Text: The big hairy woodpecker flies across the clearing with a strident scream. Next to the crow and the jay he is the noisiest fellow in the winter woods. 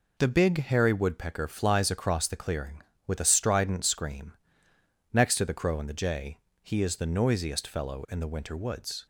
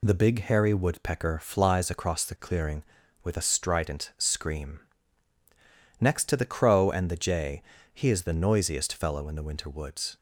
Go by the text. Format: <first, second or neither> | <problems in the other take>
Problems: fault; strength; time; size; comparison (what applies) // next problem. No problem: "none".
neither | pauses between "jay" and "he"; slight; the same in both